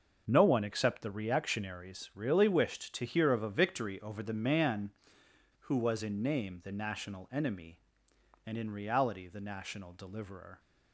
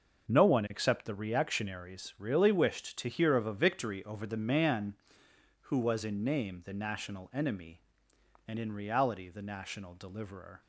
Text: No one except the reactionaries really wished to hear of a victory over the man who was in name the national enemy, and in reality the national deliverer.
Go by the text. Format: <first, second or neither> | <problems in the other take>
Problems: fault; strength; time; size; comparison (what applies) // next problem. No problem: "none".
neither | starts louder than the rest; the same in both